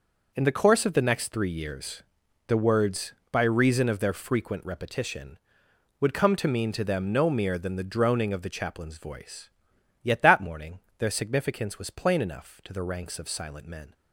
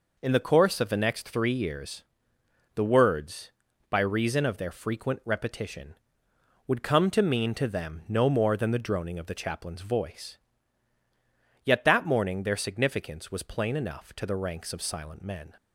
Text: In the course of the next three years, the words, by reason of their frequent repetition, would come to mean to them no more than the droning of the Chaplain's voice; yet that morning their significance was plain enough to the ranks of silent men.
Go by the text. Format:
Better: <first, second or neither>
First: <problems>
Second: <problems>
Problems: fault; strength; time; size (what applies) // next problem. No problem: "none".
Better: second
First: says "mere" for "more"; at 7.2 s // pauses between "morning" and "their"; slight; at 10.7 s; 0.18 s long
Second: none